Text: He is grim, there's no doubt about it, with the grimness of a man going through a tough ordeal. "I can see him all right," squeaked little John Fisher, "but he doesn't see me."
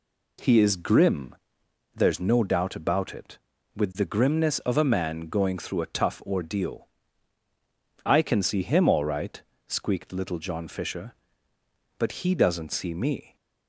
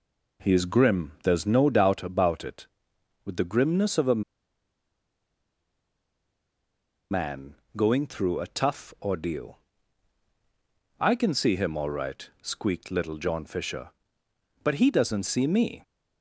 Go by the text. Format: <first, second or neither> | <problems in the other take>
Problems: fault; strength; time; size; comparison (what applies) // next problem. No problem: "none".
first | pauses between "a" and "man"; strong; at 4.2 s; 2.9 s long // pauses between "man" and "going"; slight; at 7.5 s; 0.22 s long